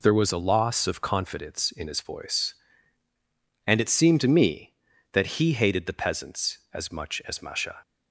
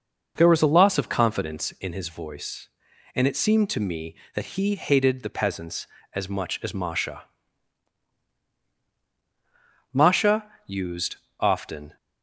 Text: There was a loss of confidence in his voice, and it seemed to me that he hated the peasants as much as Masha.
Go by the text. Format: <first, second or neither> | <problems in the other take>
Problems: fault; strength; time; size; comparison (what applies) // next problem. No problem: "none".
first | goes on to say "Masha used often"; strong; from 9.9 s on; 2.0 s long